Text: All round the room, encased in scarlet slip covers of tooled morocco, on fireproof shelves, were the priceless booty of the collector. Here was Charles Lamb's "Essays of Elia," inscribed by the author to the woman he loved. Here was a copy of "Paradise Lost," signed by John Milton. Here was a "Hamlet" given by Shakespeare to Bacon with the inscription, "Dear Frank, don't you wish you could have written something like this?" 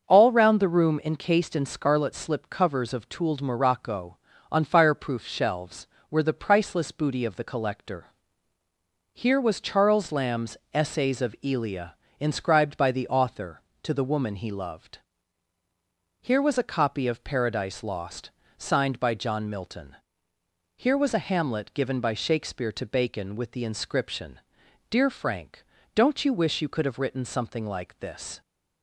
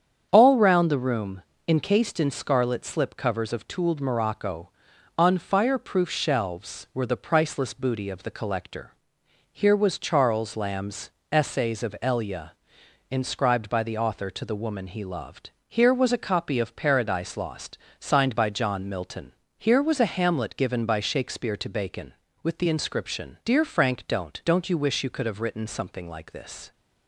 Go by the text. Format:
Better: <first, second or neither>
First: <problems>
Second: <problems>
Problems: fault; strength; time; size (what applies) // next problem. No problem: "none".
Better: first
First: starts louder than the rest; until 1.1 s; 6.5 dB // pauses between "Lamb's" and "Essays"; slight; at 10.5 s; 0.16 s long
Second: starts louder than the rest; strong; until 1.3 s; 8 dB // pauses between "Lamb's" and "Essays"; slight; at 11.0 s; 0.24 s long // says "don't" twice; at 24.4 s